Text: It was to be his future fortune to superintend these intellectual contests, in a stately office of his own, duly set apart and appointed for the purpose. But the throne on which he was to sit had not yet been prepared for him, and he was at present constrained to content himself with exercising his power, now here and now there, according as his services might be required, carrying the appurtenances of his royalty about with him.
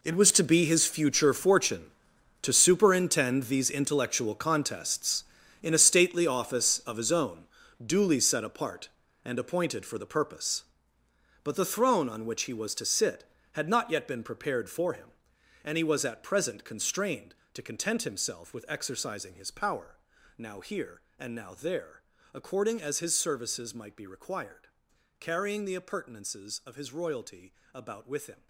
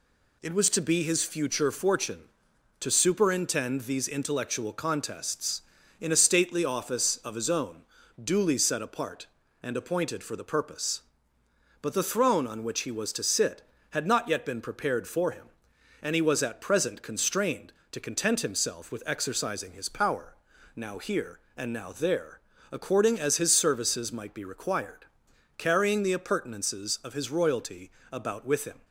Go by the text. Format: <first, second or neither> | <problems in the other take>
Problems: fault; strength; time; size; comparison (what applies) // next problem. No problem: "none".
second | gets quieter; strong; throughout; 15.5 dB // pauses between "royalty" and "about"; slight; at 27.5 s; 0.22 s long; slight in the second